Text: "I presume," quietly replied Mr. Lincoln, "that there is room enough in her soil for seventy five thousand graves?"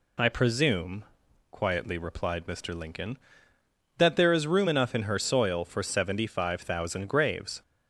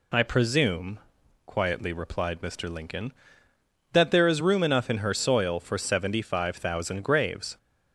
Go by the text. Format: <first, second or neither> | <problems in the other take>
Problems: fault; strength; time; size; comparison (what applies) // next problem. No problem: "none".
neither | none